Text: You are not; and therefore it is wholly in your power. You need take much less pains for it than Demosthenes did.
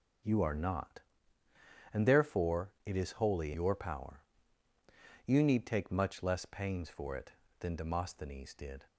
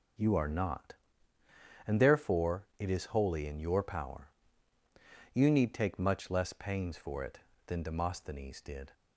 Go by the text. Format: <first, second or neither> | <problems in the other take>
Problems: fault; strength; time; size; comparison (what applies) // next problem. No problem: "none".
second | skips "in"; at 3.5 s